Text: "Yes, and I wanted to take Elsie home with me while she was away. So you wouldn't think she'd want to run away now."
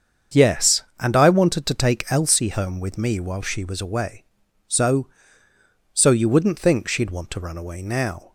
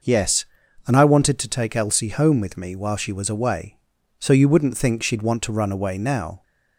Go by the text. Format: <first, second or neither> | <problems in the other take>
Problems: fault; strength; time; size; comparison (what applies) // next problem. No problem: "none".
second | starts louder than the rest; strong; until 1.5 s; 7 dB // says "So" twice; at 5.9 s